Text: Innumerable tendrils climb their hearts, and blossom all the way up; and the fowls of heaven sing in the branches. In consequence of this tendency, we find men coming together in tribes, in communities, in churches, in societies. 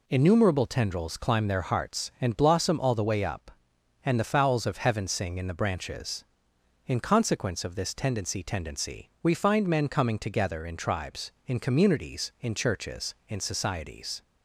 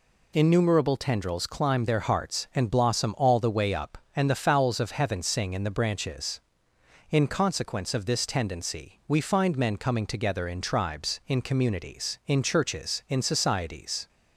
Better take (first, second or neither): second